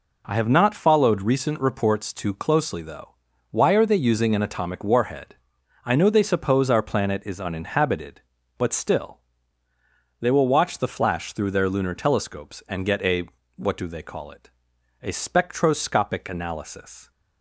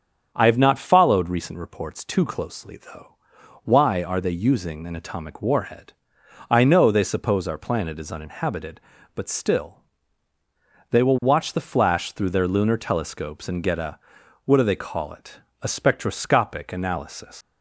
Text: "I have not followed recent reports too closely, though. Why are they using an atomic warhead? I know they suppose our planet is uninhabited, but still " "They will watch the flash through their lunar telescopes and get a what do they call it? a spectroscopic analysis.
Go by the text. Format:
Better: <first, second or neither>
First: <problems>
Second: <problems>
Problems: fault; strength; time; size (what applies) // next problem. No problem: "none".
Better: first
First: pauses between "a" and "what"; slight; at 13.2 s; 0.28 s long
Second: starts louder than the rest; strong; until 1.3 s; 7.5 dB // pauses between "a" and "what"; at 13.9 s; 0.44 s long // leaves "analysis" unfinished; at 17.4 s; 190 ms